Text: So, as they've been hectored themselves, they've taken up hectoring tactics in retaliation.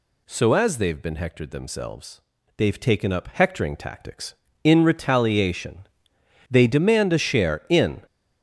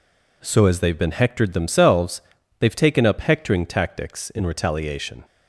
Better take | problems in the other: second | goes on to say "They demand a share in"; from 6.5 s on; 1.5 s long

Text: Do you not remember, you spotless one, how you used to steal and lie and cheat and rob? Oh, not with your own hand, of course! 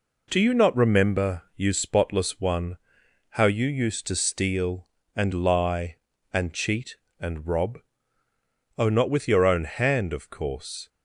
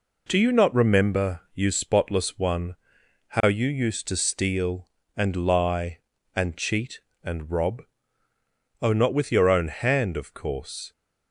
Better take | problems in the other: neither | none

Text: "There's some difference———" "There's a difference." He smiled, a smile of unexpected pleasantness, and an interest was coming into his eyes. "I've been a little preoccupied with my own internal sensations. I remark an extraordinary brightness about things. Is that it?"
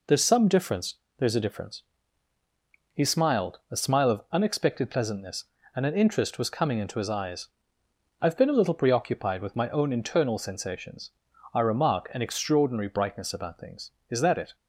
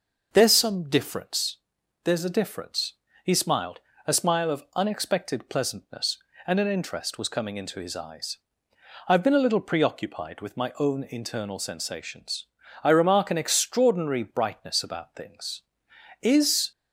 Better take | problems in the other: first | stops before "that it"; at 16.7 s

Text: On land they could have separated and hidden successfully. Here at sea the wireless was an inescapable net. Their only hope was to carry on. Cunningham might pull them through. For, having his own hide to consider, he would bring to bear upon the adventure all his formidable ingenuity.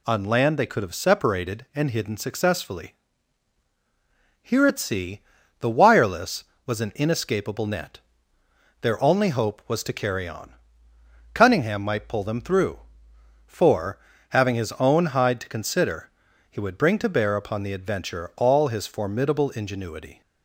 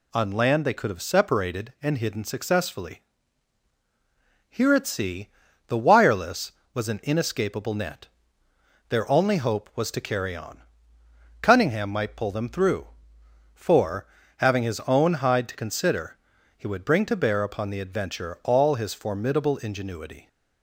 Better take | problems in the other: neither | pauses between "sea" and "the"; the same in both

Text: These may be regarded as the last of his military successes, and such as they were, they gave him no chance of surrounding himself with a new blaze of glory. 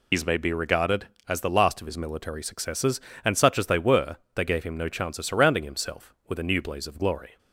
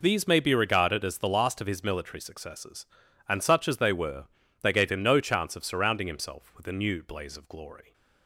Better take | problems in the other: second | loses the start of "These"; at 0.1 s; 105 ms

